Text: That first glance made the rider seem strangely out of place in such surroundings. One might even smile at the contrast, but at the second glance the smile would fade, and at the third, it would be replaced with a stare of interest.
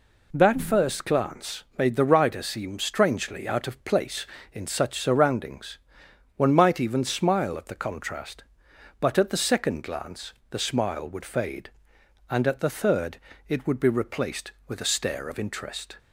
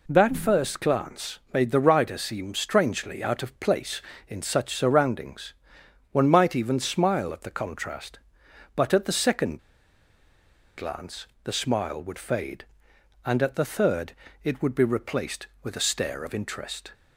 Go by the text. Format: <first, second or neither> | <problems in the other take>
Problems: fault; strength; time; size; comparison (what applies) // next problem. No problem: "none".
first | pauses between "second" and "glance"; at 9.5 s; 1.1 s long // pauses between "glance" and "the"; slight; at 11.2 s; 0.18 s long; slight in the first